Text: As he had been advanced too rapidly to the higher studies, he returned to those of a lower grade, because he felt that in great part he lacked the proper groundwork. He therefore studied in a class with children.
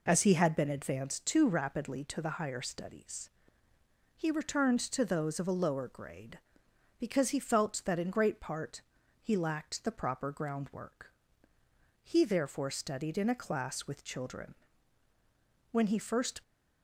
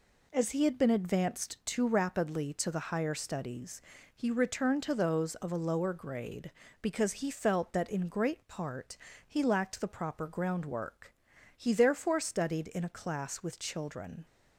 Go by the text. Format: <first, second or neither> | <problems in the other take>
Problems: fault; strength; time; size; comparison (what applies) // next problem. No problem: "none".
second | pauses between "part" and "he"; at 8.8 s; 0.40 s long; slight in the second // goes on to say "When he first"; noticeable; from 15.7 s on; 0.68 s long